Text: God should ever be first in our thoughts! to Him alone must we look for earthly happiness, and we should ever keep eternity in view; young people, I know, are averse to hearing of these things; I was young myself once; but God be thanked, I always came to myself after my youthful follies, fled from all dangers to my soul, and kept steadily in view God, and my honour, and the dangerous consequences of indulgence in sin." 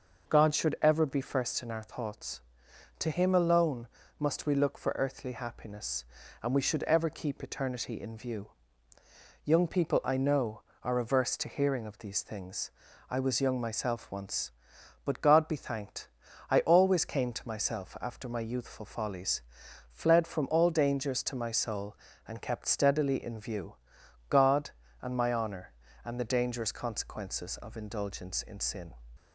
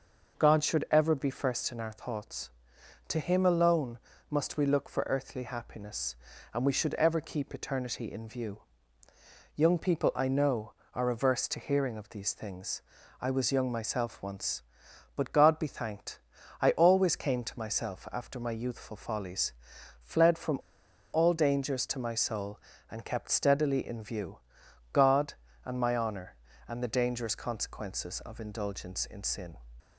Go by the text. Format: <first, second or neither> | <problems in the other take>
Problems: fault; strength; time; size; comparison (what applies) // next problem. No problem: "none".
first | pauses between "alone" and "must"; slight; at 3.9 s; 0.30 s long; slight in the first // pauses between "from" and "all"; noticeable; at 20.5 s; 0.54 s long // pauses between "view" and "God"; noticeable; at 24.3 s; 0.54 s long; noticeable in the first